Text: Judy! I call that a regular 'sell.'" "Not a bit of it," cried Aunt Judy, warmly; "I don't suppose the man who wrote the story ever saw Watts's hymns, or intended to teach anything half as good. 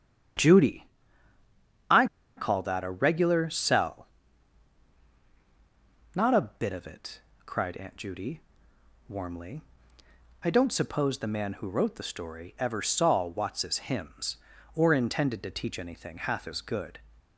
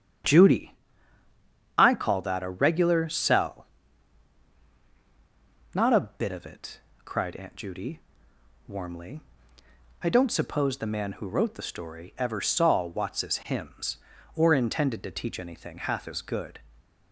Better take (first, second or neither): second